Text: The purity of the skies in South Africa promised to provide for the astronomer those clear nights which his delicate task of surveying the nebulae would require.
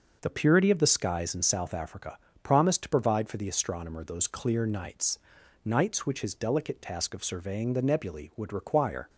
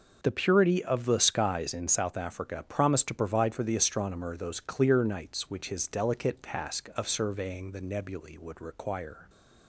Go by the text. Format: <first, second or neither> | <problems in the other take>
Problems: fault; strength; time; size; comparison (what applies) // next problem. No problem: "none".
second | pauses between "Africa" and "promised"; slight; at 2.1 s; 0.24 s long // says "nights" twice; at 5.6 s